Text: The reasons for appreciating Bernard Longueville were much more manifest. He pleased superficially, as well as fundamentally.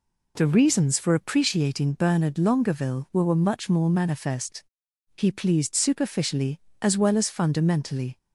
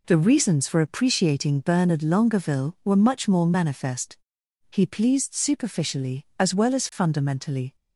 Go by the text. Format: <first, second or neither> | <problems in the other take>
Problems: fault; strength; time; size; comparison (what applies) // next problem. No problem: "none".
second | says "were" twice; at 3.2 s